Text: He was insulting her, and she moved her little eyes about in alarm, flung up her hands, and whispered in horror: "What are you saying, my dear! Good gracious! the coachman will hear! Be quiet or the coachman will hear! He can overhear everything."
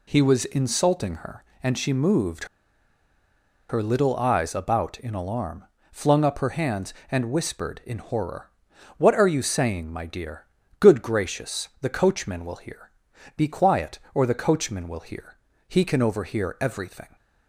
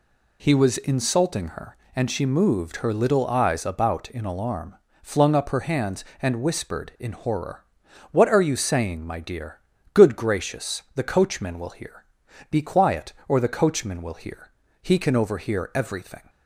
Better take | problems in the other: second | pauses between "moved" and "her"; at 2.4 s; 1.2 s long

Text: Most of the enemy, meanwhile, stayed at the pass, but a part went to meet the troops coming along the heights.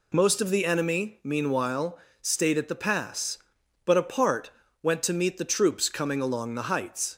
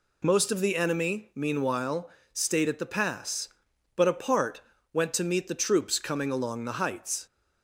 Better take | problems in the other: neither | pauses between "part" and "went"; slight; the same in both

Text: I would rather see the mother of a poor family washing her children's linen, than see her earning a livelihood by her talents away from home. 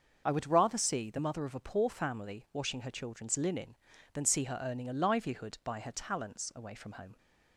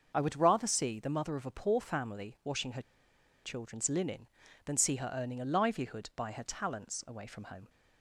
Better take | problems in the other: first | starts louder than the rest; until 1.1 s; 6.5 dB; also in the first // pauses between "her" and "children's"; noticeable; at 2.8 s; 0.63 s long

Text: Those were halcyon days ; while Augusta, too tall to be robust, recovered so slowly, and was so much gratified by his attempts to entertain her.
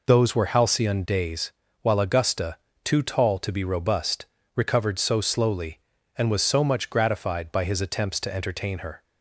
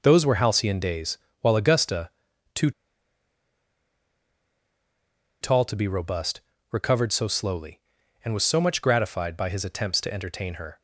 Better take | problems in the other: first | pauses between "too" and "tall"; strong; at 2.7 s; 2.7 s long

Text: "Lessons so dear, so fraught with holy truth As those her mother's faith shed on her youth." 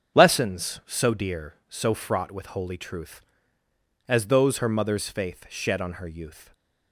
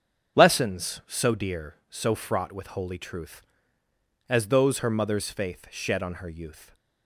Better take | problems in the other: neither | starts louder than the rest; strong; the same in both

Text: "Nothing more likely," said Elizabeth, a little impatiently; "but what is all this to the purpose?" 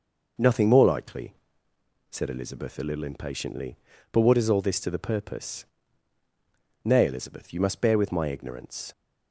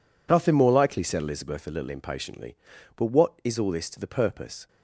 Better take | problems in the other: second | goes on to say "Nay Elizabeth you must bear with my ignorance"; strong; from 6.8 s on; 2.0 s long

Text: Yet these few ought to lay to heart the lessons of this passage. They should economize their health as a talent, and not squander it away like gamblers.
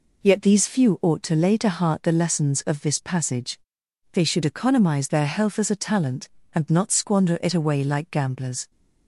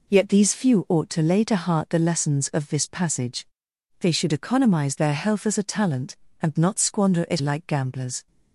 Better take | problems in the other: first | skips "away"; at 7.4 s

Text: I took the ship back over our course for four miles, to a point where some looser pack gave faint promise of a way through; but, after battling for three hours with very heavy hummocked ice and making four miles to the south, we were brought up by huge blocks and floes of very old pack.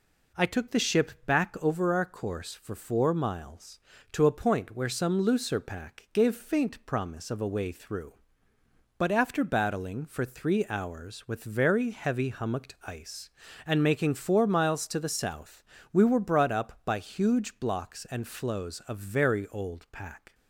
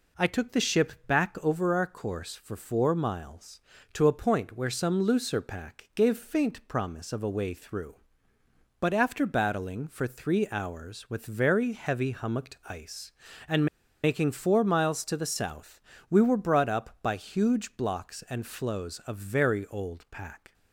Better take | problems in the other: first | pauses between "and" and "making"; at 13.6 s; 0.37 s long

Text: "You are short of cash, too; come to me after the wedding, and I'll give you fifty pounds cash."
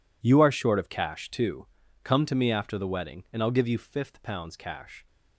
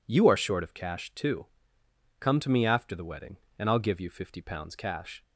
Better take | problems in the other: second | says "fifth" for "fifty"; at 3.7 s

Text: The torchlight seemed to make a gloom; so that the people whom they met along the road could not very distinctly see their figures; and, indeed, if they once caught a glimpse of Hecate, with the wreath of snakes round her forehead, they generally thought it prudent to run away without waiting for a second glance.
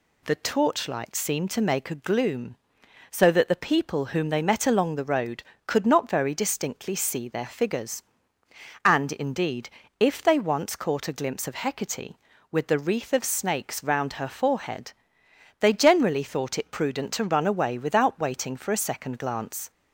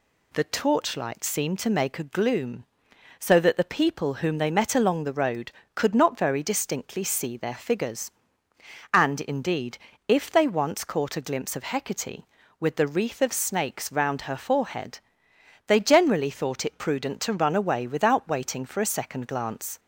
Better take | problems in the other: neither | none

